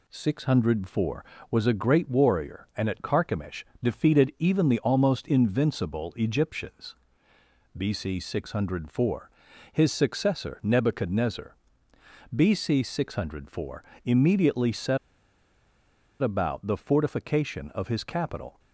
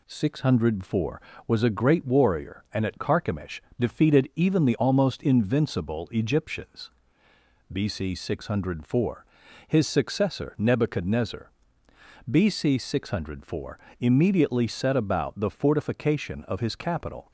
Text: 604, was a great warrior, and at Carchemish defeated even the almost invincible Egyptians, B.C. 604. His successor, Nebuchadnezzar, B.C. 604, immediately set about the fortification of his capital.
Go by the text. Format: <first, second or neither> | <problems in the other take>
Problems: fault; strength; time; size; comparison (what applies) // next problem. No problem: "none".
second | pauses between "Carchemish" and "defeated"; slight; at 3.6 s; 0.18 s long; slight in the second // pauses between "set" and "about"; strong; at 14.9 s; 1.2 s long